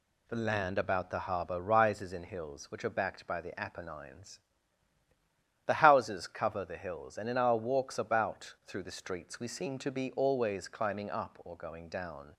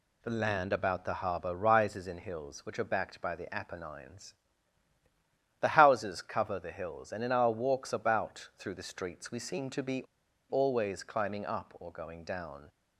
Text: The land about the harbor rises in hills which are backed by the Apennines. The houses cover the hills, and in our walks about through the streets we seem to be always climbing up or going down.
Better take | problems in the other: first | pauses between "be" and "always"; noticeable; at 10.0 s; 0.49 s long

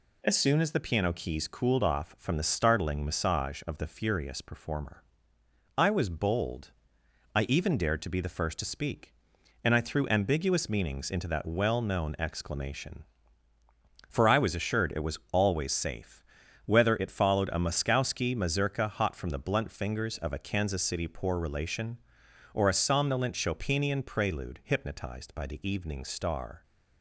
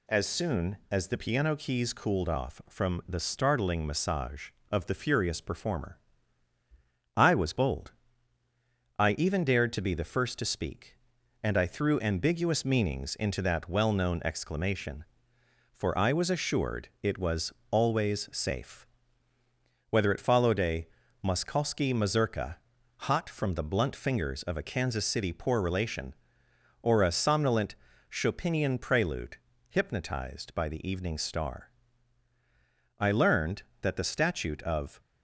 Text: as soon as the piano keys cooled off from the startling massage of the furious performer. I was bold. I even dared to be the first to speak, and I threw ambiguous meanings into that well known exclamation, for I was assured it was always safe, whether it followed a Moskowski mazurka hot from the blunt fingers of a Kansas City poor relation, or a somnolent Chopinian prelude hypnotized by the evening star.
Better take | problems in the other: first | pauses between "was" and "always"; slight; at 17.5 s; 0.18 s long // pauses between "a" and "Moskowski"; at 20.8 s; 0.38 s long // pauses between "mazurka" and "hot"; at 22.5 s; 0.44 s long // pauses between "somnolent" and "Chopinian"; slight; at 27.7 s; 0.36 s long // pauses between "prelude" and "hypnotized"; slight; at 29.3 s; 0.32 s long // goes on to say "I learned that the statute of"; strong; from 32.9 s on; 2.0 s long

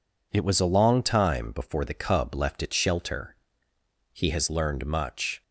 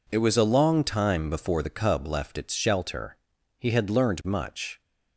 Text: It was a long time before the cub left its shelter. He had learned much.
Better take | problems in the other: second | says "has" for "had"; at 4.3 s

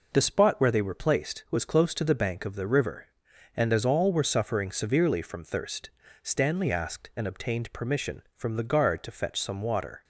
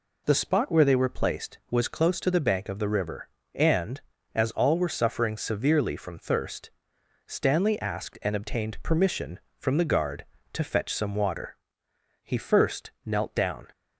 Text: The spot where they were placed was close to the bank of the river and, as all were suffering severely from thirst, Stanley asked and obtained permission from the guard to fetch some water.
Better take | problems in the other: first | goes on to say "He first knelt down"; from 12.2 s on; 1.4 s long

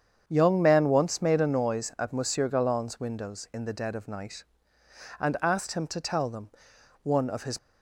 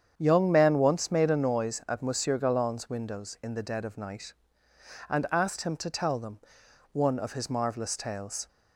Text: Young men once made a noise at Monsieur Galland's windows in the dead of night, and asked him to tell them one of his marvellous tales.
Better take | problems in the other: second | starts louder than the rest; strong; until 1.2 s; 7.5 dB; strong in the second // pauses between "them" and "one"; noticeable; at 6.4 s; 0.54 s long; noticeable in the second // stops before "marvellous tales"; at 7.5 s

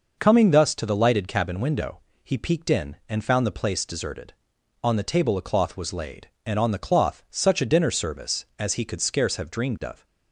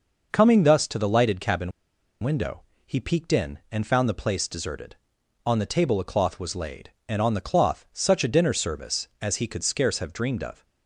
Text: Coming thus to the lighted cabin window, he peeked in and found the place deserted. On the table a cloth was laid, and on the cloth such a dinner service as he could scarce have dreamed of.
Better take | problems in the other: first | pauses between "cabin" and "window"; noticeable; at 1.7 s; 0.51 s long

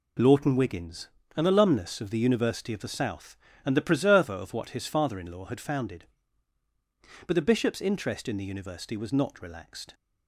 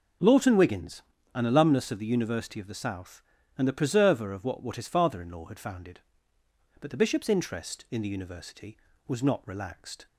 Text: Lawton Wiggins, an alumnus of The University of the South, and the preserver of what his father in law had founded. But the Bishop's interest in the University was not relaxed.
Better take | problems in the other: first | says "what" twice; at 4.6 s

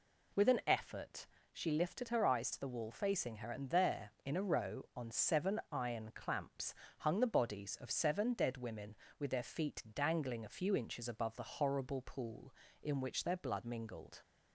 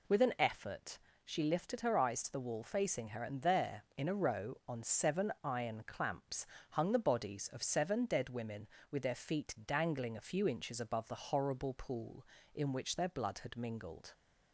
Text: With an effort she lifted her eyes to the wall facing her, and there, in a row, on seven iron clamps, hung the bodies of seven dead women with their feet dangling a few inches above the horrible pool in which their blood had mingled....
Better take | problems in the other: second | pauses between "effort" and "she"; slight; at 1.2 s; 0.26 s long; slight in the second // skips "had"; at 13.6 s

